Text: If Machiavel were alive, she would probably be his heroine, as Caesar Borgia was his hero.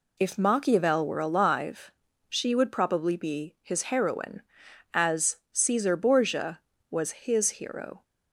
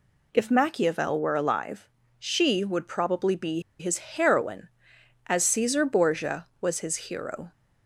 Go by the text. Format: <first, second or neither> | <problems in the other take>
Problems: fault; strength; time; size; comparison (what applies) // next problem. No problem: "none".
first | pauses between "be" and "his"; slight; at 3.6 s; 0.19 s long